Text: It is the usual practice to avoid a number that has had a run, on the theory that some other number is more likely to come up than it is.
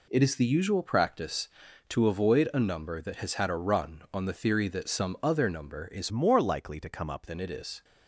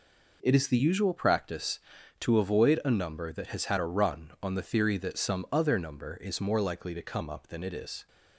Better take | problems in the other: second | changes voice from "more" to "up"; from 6.0 to 7.2 s; 1.2 s long

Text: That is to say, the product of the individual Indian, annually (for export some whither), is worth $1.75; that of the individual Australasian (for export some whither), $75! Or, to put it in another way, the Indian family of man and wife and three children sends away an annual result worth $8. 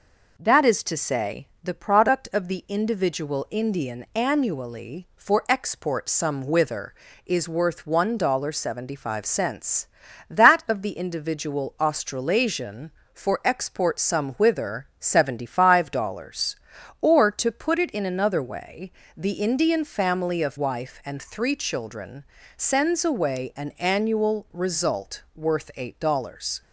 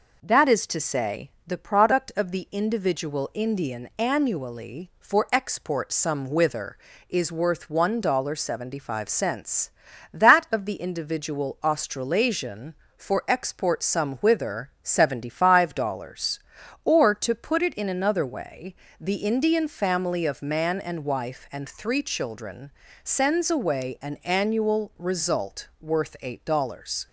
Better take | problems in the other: second | skips "man and"; at 20.5 s // pauses between "children" and "sends"; slight; at 22.2 s; 0.32 s long; slight in the second

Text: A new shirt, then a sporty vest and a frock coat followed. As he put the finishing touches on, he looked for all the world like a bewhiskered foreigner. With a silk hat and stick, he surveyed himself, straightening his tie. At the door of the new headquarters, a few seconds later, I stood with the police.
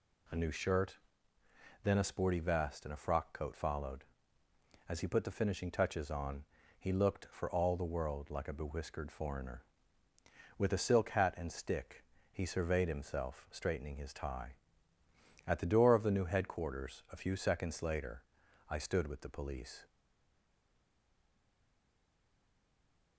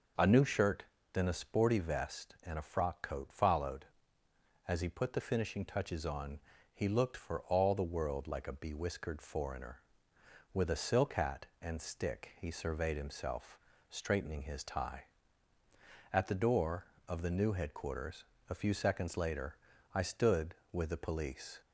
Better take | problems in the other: second | stays silent after the last word; strong; from 19.8 s on; 3.3 s long

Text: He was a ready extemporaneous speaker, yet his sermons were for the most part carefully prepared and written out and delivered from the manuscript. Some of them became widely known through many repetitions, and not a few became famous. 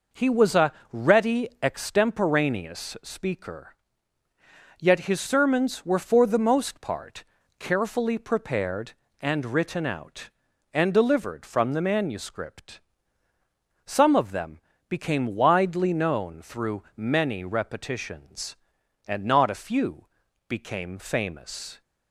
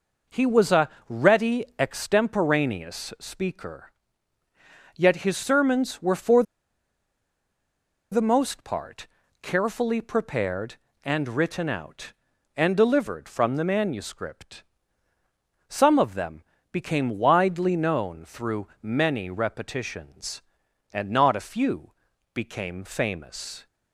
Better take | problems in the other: first | pauses between "a" and "ready"; slight; at 0.8 s; 0.20 s long; slight in the first // pauses between "for" and "the"; strong; at 6.4 s; 1.6 s long // pauses between "part" and "carefully"; slight; at 9.0 s; 0.36 s long; slight in the first // pauses between "them" and "became"; slight; at 16.4 s; 0.30 s long; slight in the first // pauses between "through" and "many"; slight; at 18.6 s; 0.16 s long // pauses between "few" and "became"; at 21.9 s; 0.42 s long; also in the first

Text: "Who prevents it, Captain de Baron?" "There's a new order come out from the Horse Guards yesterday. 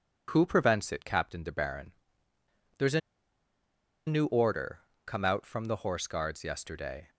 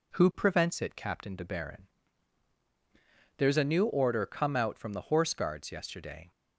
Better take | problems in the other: second | pauses between "a" and "new"; at 3.0 s; 1.0 s long // pauses between "order" and "come"; slight; at 4.7 s; 0.24 s long

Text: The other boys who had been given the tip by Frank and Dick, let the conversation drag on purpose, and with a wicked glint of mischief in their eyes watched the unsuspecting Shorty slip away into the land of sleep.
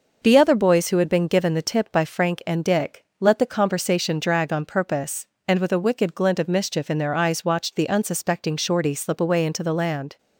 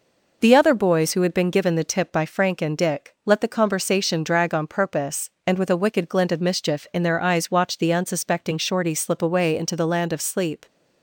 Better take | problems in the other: second | stops before "of sleep"; at 10.1 s

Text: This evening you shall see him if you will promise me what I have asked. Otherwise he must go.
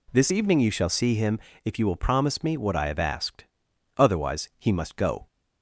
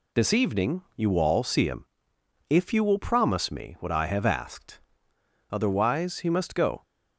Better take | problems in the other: first | says "all" for "shall"; at 1.1 s // pauses between "him" and "if"; noticeable; at 1.8 s; 0.64 s long; slight in the first

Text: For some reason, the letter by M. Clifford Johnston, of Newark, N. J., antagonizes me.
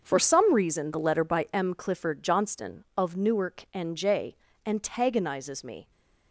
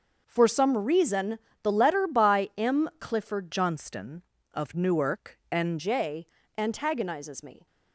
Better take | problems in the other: first | starts louder than the rest; until 1.2 s; 6.5 dB; also in the first // changes voice from "Johnston" to "N"; from 3.4 to 5.7 s; 2.3 s long

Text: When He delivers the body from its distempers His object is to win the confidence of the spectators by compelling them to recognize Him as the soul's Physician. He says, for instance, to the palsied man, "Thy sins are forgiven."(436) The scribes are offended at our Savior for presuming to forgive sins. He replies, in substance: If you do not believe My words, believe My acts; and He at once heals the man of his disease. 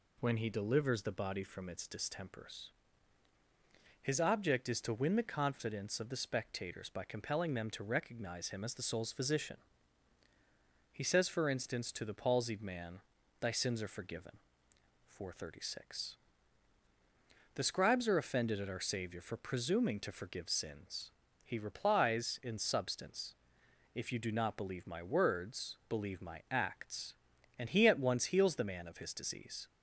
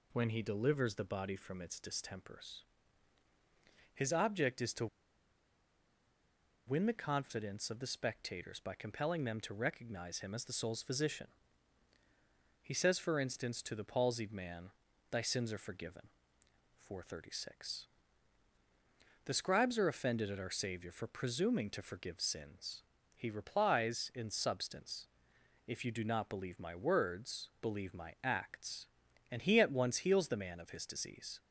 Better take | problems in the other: first | pauses between "distempers" and "His"; strong; at 2.6 s; 1.3 s long; strong in the first // pauses between "to" and "win"; strong; at 4.8 s; 1.8 s long

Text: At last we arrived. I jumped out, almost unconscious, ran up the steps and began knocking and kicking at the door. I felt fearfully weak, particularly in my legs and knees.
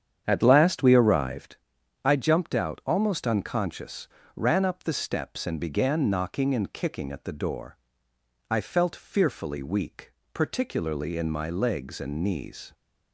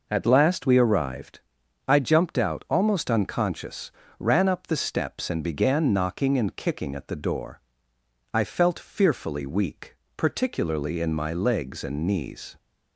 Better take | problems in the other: second | starts louder than the rest; strong; until 1.7 s; 8.5 dB

